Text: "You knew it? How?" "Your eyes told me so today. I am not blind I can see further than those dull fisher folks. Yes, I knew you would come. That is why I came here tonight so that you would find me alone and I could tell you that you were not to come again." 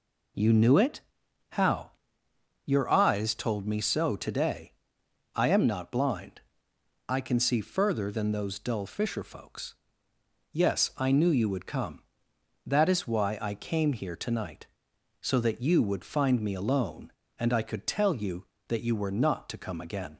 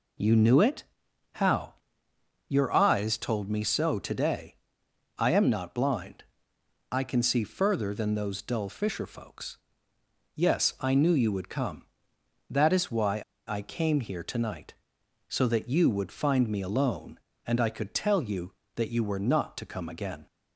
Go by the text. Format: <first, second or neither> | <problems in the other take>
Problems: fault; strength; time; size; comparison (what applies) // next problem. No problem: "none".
first | pauses between "blind" and "I"; noticeable; at 6.2 s; 0.66 s long; noticeable in the first // pauses between "why" and "I"; slight; at 13.2 s; 0.25 s long